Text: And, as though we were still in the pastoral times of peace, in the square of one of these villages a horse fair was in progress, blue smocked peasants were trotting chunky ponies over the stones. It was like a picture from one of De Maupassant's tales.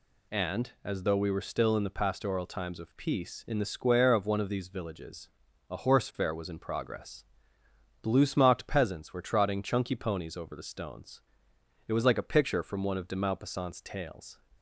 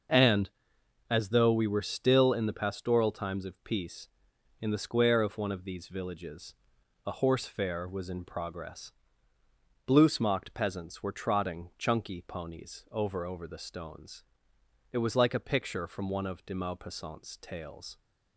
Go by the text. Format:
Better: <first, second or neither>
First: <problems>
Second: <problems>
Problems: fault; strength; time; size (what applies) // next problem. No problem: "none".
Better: first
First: pauses between "villages" and "a"; at 5.2 s; 0.42 s long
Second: starts louder than the rest; noticeable; until 1.6 s; 6 dB // pauses between "villages" and "a"; noticeable; at 6.5 s; 0.52 s long // says "over" twice; at 13.2 s